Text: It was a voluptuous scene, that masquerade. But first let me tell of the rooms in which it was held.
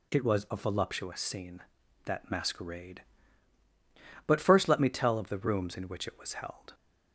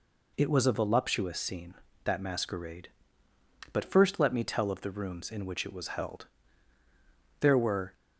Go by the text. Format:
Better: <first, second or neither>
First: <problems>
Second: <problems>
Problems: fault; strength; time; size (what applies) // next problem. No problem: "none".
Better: first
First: none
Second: goes on to say "There were"; from 7.4 s on; 0.52 s long